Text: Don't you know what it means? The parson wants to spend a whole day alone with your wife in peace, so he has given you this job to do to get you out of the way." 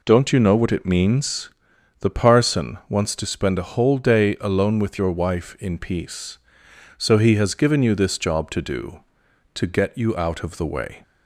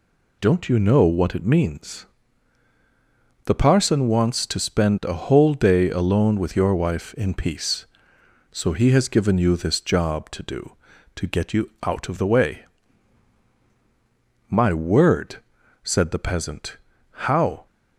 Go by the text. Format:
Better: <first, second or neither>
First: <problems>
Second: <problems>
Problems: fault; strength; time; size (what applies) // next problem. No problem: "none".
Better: first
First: none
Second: goes on to say "My word said the peasant How"; strong; from 14.4 s on; 3.1 s long